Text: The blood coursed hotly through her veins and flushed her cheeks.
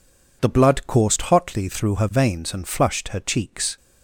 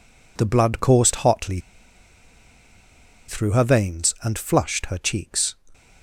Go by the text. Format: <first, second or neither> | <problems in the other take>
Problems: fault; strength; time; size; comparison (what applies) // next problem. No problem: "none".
first | pauses between "hotly" and "through"; strong; at 1.6 s; 1.6 s long